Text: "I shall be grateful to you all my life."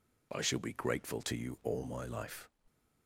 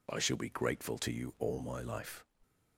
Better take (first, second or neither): neither